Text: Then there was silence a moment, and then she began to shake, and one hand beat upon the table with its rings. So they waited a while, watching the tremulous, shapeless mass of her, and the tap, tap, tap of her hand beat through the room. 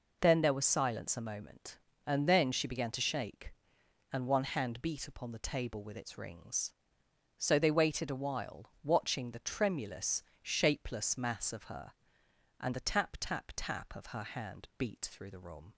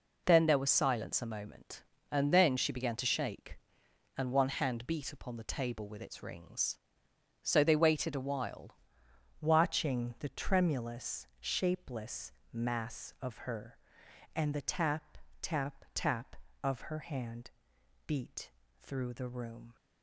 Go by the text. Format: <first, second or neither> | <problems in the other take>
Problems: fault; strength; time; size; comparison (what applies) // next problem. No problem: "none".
first | changes voice at "watching"; from 9.4 s on; 10.3 s long // pauses between "shapeless" and "mass"; slight; at 12.3 s; 0.22 s long // pauses between "hand" and "beat"; noticeable; at 17.4 s; 0.58 s long // pauses between "beat" and "through"; slight; at 18.4 s; 0.30 s long